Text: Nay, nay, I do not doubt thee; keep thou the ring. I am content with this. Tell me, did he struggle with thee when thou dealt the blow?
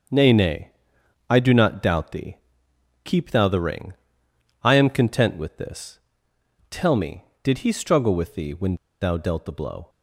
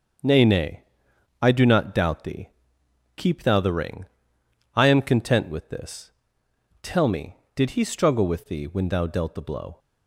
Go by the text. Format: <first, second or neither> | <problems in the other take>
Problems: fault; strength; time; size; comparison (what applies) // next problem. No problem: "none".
second | starts louder than the rest; until 1.6 s; 6.5 dB; also in the second // pauses between "when" and "thou"; slight; at 8.7 s; 0.26 s long